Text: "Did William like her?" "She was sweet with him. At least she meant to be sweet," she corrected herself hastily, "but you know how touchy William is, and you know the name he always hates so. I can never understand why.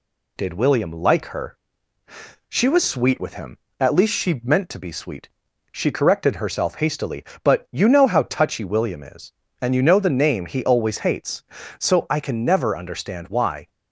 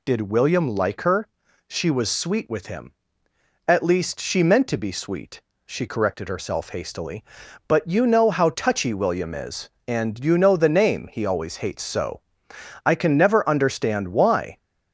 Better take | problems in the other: neither | none

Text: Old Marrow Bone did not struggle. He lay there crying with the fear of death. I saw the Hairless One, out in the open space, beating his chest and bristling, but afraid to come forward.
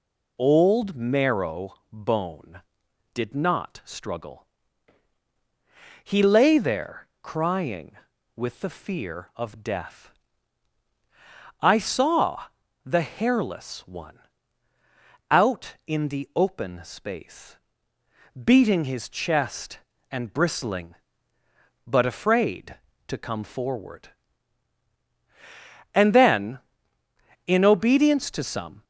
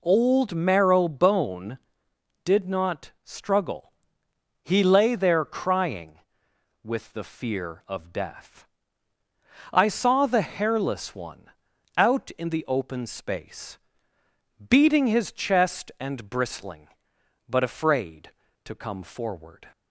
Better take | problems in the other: second | pauses between "Marrow" and "Bone"; slight; at 1.7 s; 0.16 s long // pauses between "there" and "crying"; slight; at 7.0 s; 0.16 s long // pauses between "saw" and "the"; at 12.4 s; 0.40 s long // goes on to say "And then in obedience to some"; strong; from 25.9 s on; 2.9 s long

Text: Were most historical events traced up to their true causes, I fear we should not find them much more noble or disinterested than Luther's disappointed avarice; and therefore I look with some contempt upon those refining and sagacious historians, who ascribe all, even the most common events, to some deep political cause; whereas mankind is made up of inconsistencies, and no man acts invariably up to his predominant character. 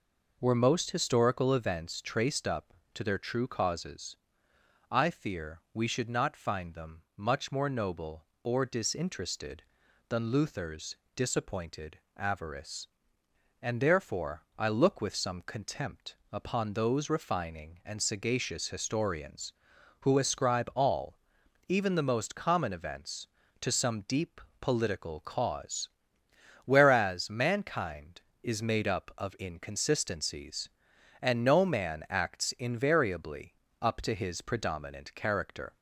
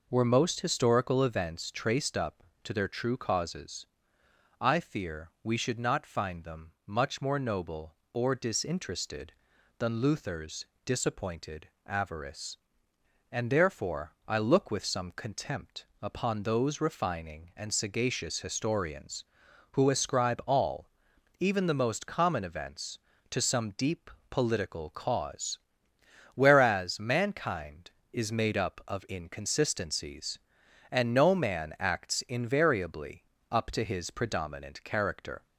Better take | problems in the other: neither | pauses between "Luther's" and "disappointed"; slight; the same in both // pauses between "disappointed" and "avarice"; slight; the same in both // pauses between "contempt" and "upon"; slight; the same in both // pauses between "deep" and "political"; slight; the same in both // pauses between "invariably" and "up"; slight; the same in both

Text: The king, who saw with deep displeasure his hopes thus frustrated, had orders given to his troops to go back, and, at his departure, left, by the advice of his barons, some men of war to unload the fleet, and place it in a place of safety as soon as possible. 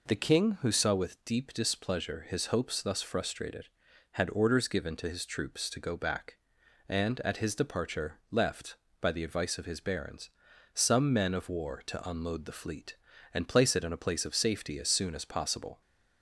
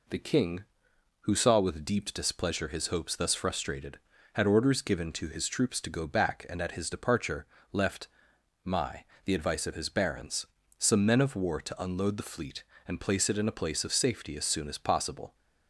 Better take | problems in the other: first | says "my" for "by"; at 8.6 s

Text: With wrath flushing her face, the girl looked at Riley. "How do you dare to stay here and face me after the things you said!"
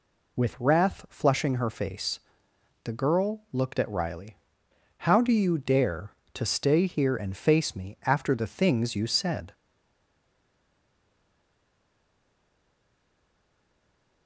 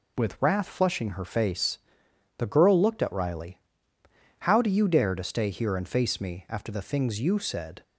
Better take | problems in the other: second | stays silent after the last word; strong; from 9.5 s on; 4.7 s long

